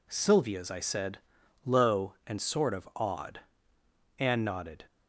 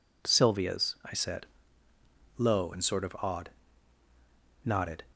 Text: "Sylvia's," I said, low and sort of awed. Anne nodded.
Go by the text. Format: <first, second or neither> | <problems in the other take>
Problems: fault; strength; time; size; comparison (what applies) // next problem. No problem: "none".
first | skips "Anne"; at 4.0 s